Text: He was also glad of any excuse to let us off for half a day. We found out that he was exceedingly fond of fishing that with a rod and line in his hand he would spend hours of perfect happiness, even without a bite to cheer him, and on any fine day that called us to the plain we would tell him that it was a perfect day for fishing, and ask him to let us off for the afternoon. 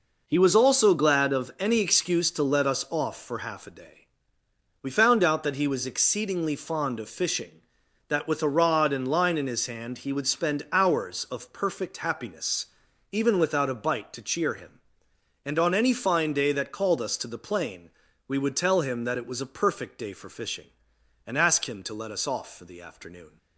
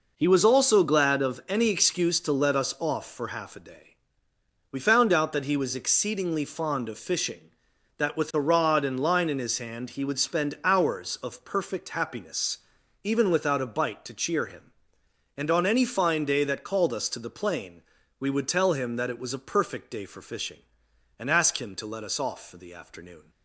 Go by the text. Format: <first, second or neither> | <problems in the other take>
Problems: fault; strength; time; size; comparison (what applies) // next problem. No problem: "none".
neither | pauses between "plain" and "we"; the same in both